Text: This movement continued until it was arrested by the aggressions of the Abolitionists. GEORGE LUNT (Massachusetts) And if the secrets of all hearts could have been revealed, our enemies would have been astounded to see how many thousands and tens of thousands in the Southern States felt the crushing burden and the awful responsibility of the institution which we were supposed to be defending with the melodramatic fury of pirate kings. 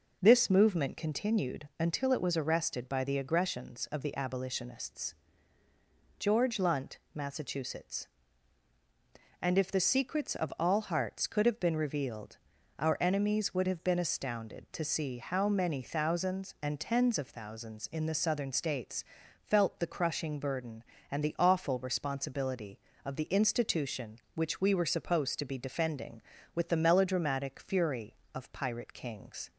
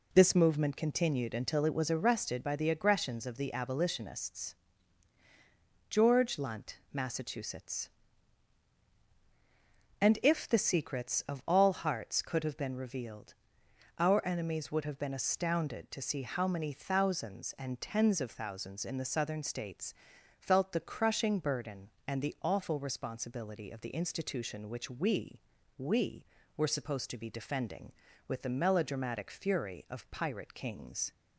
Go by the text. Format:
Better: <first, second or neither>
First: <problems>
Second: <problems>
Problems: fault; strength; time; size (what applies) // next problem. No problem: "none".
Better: first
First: pauses between "States" and "felt"; at 19.0 s; 0.40 s long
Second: pauses between "States" and "felt"; noticeable; at 19.9 s; 0.48 s long // says "we" twice; at 25.7 s